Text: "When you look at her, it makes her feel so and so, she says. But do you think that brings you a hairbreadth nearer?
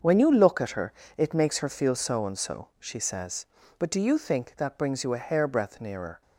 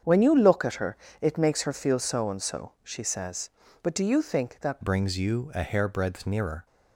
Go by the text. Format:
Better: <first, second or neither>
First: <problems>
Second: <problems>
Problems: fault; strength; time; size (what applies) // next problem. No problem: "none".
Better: first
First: starts louder than the rest; until 1.2 s; 6.5 dB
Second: starts louder than the rest; strong; until 1.2 s; 7.5 dB // changes voice at "brings"; from 4.8 s on; 1.8 s long